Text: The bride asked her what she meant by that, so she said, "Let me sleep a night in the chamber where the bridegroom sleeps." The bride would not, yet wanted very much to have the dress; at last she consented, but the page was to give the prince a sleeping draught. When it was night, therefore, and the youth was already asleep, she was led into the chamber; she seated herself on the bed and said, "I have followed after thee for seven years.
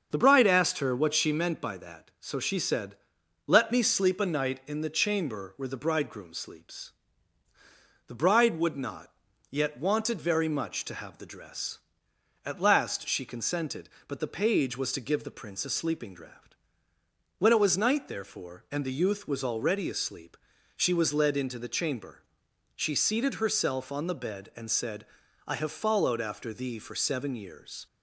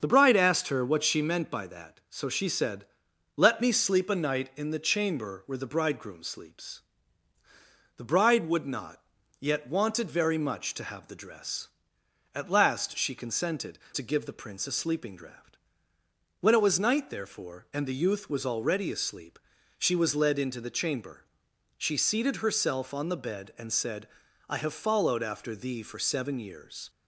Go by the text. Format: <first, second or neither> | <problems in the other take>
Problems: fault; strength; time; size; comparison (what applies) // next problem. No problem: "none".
first | starts louder than the rest; until 1.0 s; 7 dB; also in the first // skips "but the page was"; at 13.8 s